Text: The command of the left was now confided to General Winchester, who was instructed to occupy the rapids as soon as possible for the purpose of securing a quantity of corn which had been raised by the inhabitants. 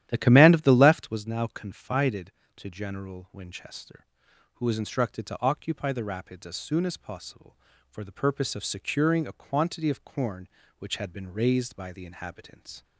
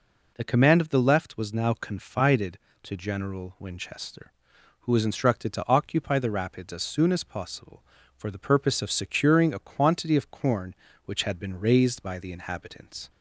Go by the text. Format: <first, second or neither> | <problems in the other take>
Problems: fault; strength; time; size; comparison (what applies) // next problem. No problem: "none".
second | starts louder than the rest; strong; until 1.2 s; 12 dB